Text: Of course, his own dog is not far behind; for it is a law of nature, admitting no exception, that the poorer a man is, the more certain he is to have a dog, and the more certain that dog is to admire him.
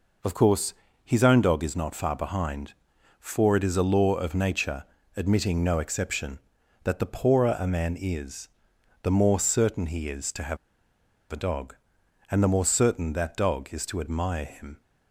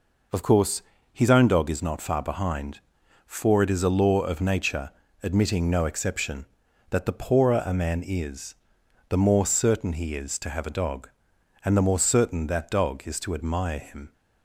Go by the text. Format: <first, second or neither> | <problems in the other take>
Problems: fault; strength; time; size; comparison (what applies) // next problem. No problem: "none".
second | pauses between "have" and "a"; noticeable; at 10.5 s; 0.74 s long